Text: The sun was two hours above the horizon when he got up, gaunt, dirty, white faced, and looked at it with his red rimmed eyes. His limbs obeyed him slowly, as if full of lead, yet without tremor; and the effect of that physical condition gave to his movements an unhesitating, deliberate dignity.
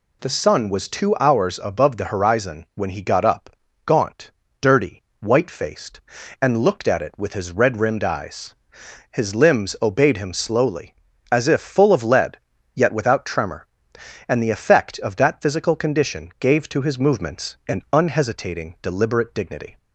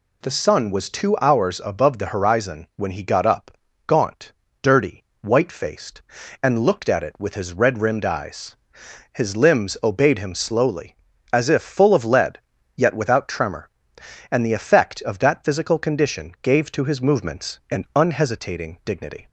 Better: first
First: none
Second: skips "deliberate"; at 18.8 s

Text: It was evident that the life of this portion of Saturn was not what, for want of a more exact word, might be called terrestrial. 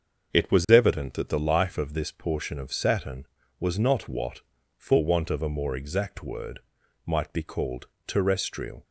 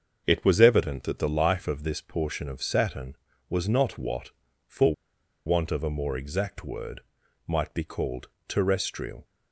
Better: first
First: starts louder than the rest; until 1.3 s; 6.5 dB // pauses between "called" and "terrestrial"; slight; at 7.8 s; 0.22 s long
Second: starts louder than the rest; until 1.2 s; 6.5 dB // pauses between "for" and "want"; noticeable; at 4.9 s; 0.52 s long // pauses between "called" and "terrestrial"; slight; at 8.2 s; 0.22 s long

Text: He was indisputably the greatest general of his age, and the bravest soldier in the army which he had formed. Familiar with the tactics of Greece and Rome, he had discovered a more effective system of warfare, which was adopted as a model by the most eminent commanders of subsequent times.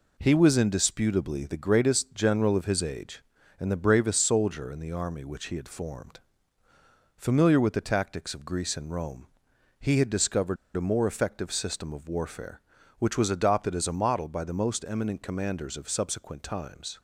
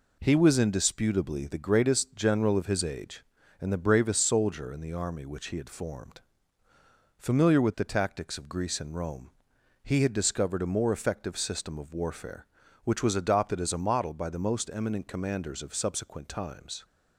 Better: second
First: pauses between "discovered" and "a"; slight; at 10.5 s; 0.21 s long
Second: none

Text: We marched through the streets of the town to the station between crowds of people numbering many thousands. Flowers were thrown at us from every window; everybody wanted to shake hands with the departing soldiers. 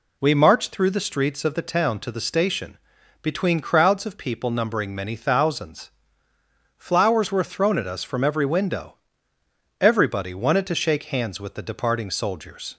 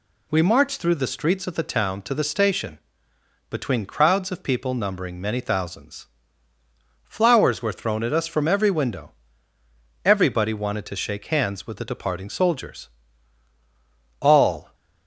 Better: first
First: pauses between "station" and "between"; at 2.7 s; 0.44 s long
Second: pauses between "station" and "between"; noticeable; at 2.7 s; 0.70 s long // goes on to say "All"; from 14.2 s on; 0.54 s long

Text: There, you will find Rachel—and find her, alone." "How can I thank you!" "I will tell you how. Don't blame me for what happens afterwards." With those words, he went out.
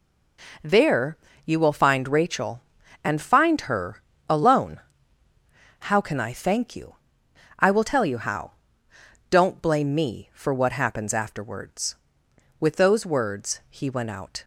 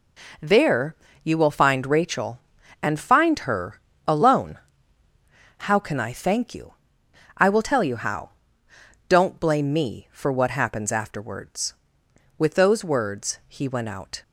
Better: neither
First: none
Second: none

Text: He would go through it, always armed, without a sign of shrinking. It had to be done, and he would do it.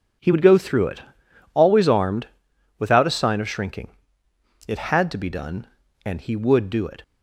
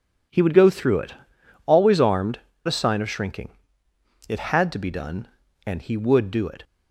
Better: first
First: none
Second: skips "without"; at 2.5 s

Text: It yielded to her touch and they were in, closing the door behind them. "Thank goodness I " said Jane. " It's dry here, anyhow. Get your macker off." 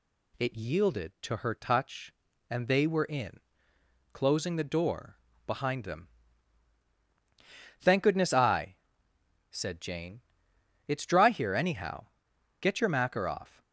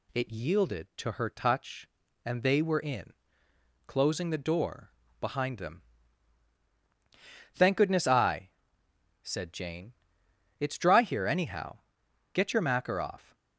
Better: neither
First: pauses between "door" and "behind"; slight; at 5.1 s; 0.30 s long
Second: pauses between "door" and "behind"; slight; at 4.9 s; 0.30 s long

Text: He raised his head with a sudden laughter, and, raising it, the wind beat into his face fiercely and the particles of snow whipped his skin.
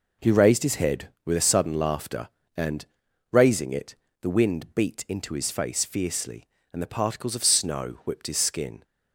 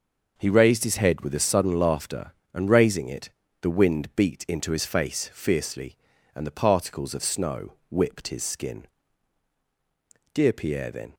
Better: first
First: none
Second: pauses between "snow" and "whipped"; slight; at 7.7 s; 0.18 s long // goes on to say "Dear Pierre then"; noticeable; from 10.3 s on; 0.80 s long

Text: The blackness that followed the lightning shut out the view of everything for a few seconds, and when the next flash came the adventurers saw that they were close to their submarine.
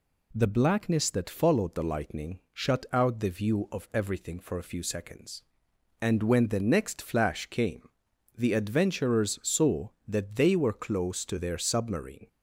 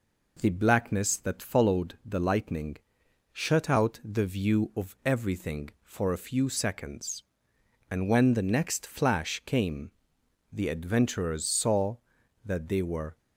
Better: first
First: pauses between "came" and "the"; noticeable; at 7.8 s; 0.48 s long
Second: pauses between "lightning" and "shut"; noticeable; at 2.7 s; 0.58 s long // pauses between "came" and "the"; noticeable; at 9.8 s; 0.62 s long // stops before "close to their submarine"; at 13.1 s

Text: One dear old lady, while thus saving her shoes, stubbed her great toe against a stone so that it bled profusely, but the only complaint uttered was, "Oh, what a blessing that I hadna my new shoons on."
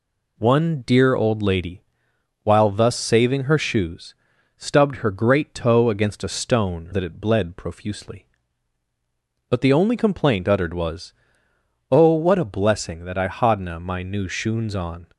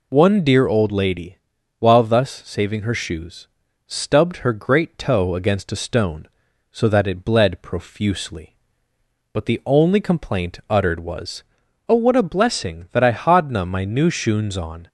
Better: second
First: skips "so"; at 6.9 s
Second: none

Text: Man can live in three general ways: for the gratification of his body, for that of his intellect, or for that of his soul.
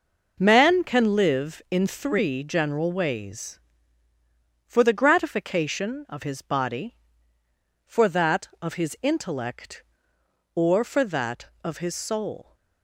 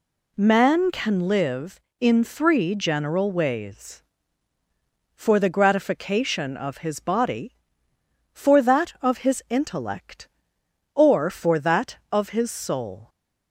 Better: neither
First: none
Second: none

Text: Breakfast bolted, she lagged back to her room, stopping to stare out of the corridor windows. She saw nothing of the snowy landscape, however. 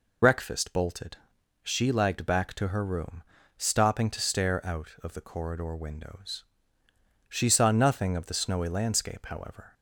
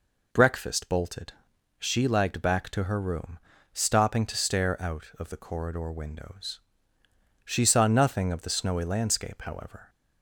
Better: second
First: loses the start of "Breakfast"; at 0.2 s; 50 ms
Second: none

